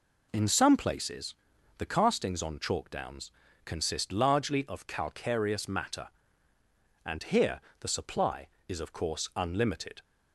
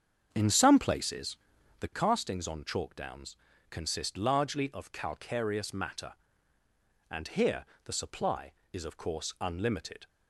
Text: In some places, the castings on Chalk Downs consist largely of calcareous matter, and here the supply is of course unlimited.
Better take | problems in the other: first | starts louder than the rest; strong; until 2.0 s; 7.5 dB // pauses between "Downs" and "consist"; slight; at 3.3 s; 0.34 s long; slight in the first // pauses between "here" and "the"; slight; at 7.6 s; 0.18 s long; slight in the first

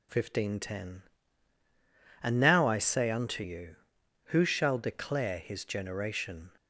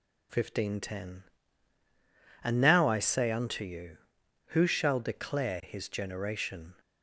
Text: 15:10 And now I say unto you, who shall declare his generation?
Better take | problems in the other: neither | none

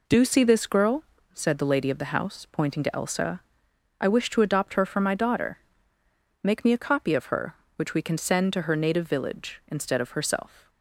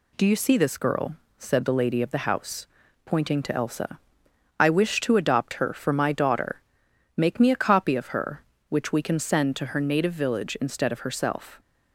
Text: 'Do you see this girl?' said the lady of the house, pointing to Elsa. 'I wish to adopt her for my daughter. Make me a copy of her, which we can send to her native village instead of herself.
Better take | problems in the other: second | skips "you"; at 0.2 s

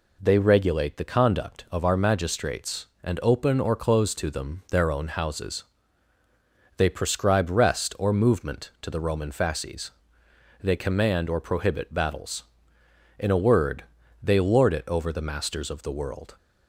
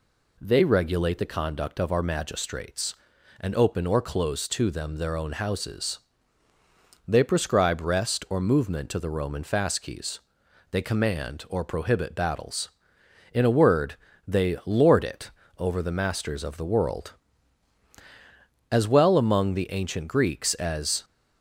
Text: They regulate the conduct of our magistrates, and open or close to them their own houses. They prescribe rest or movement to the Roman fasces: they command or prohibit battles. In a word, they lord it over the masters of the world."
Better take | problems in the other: first | pauses between "it" and "over"; slight; at 15.3 s; 0.26 s long // goes on to say "As well among the ancient Greeks as"; strong; from 18.7 s on; 2.3 s long

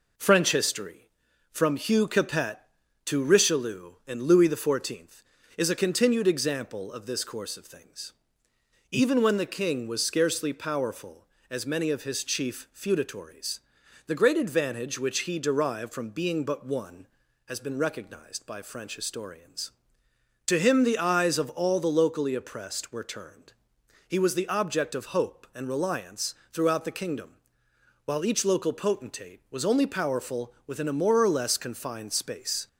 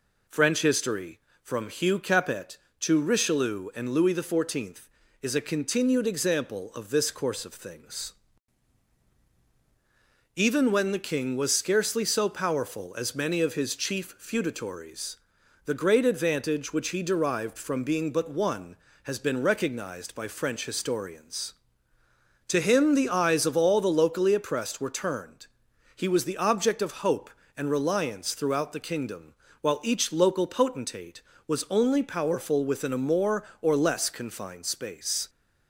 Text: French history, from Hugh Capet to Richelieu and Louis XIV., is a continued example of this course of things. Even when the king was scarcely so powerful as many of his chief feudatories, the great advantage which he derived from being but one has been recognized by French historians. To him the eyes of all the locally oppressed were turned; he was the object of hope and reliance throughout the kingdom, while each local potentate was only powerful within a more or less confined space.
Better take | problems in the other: second | skips "so"; at 10.5 s // pauses between "reliance" and "throughout"; slight; at 26.3 s; 0.18 s long

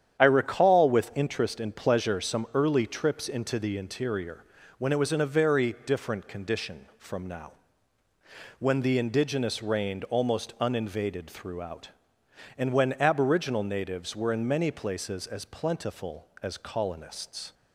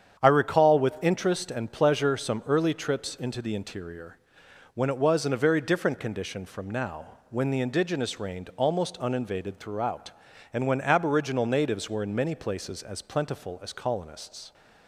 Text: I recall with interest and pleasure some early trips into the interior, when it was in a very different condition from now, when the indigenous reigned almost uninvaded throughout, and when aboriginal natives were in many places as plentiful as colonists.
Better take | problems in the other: neither | starts louder than the rest; strong; the same in both

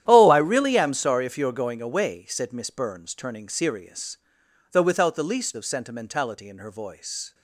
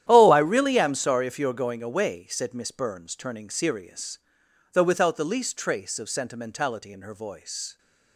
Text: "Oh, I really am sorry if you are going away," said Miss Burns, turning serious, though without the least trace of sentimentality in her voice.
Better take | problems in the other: second | starts louder than the rest; strong; until 1.0 s; 11 dB; strong in the second // skips "trace"; at 5.5 s

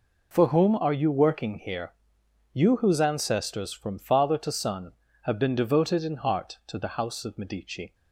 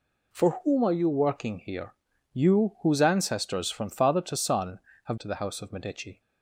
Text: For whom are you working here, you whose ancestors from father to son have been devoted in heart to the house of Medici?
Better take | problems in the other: first | skips "been devoted in heart"; at 5.1 s

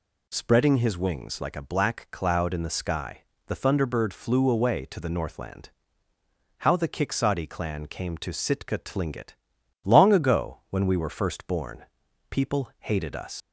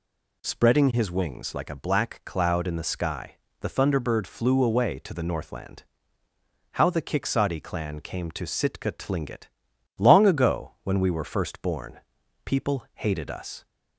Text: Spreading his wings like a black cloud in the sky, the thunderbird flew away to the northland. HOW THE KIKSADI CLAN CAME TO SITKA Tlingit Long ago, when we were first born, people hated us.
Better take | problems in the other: second | pauses between "Tlingit" and "Long"; noticeable; at 9.3 s; 0.50 s long; noticeable in the second // leaves "us" unfinished; at 13.4 s; 100 ms

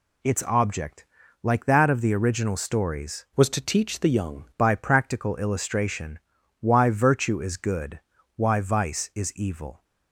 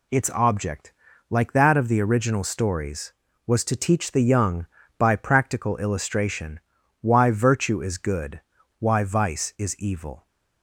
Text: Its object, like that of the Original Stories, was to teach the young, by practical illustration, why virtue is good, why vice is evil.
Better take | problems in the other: second | changes voice from "was" to "young"; from 3.3 to 4.4 s; 1.1 s long

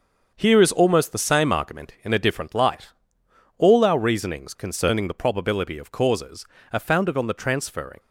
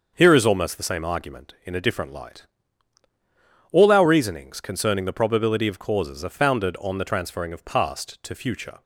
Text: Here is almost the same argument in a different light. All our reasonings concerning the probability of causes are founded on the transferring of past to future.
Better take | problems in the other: second | starts louder than the rest; until 1.3 s; 6.5 dB; also in the second // stops before "of past to future"; at 7.9 s

